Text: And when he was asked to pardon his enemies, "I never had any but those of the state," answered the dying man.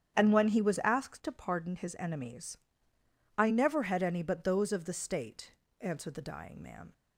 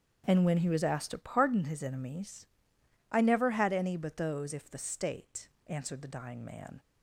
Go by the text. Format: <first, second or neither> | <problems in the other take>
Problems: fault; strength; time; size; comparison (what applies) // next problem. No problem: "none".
first | starts louder than the rest; strong; until 1.2 s; 7.5 dB; strong in the first // says "if" for "of"; at 4.5 s